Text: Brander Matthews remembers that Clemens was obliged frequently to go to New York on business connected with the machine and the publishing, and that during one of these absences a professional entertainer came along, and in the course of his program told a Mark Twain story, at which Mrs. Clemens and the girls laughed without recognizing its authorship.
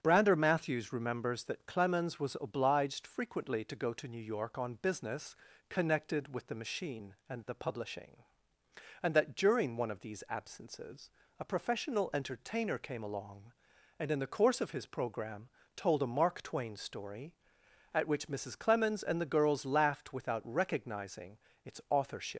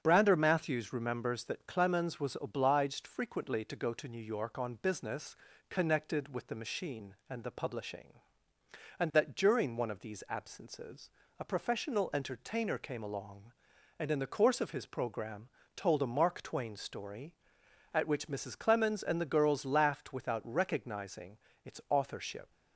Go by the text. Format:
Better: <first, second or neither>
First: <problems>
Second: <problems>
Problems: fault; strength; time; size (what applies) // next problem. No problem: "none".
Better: second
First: starts louder than the rest; strong; until 1.0 s; 8 dB // pauses between "business" and "connected"; slight; at 5.3 s; 0.34 s long // pauses between "absences" and "a"; slight; at 11.1 s; 0.28 s long // pauses between "program" and "told"; slight; at 15.4 s; 0.28 s long // pauses between "recognizing" and "its"; slight; at 21.3 s; 0.28 s long // leaves "authorship" unfinished; at 22.3 s; 125 ms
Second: starts louder than the rest; strong; until 1.0 s; 8 dB // pauses between "business" and "connected"; slight; at 5.3 s; 0.34 s long // pauses between "absences" and "a"; slight; at 11.1 s; 0.28 s long // pauses between "program" and "told"; slight; at 15.4 s; 0.28 s long // pauses between "recognizing" and "its"; slight; at 21.3 s; 0.28 s long